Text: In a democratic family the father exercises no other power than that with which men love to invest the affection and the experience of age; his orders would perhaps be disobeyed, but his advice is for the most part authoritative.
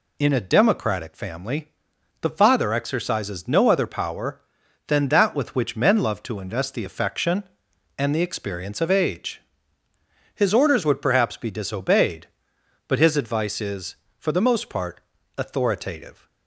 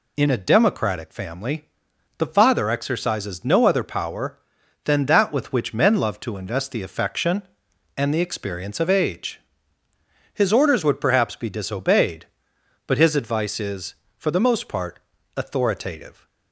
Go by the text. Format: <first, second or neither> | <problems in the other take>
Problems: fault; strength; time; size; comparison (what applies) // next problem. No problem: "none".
neither | pauses between "family" and "the"; noticeable; the same in both // pauses between "part" and "authoritative"; the same in both